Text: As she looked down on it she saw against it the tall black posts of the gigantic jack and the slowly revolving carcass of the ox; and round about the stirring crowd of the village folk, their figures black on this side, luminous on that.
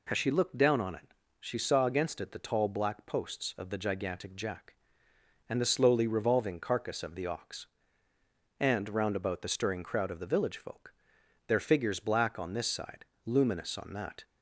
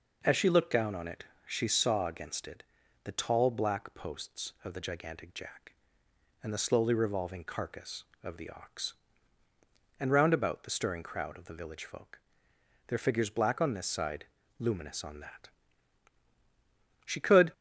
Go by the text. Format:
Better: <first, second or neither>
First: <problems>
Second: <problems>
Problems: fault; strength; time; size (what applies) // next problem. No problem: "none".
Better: first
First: pauses between "it" and "she"; slight; at 1.1 s; 0.26 s long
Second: pauses between "it" and "she"; slight; at 1.2 s; 0.24 s long // pauses between "it" and "the"; at 2.6 s; 0.44 s long // goes on to say "She could"; slight; from 17.0 s on; 0.48 s long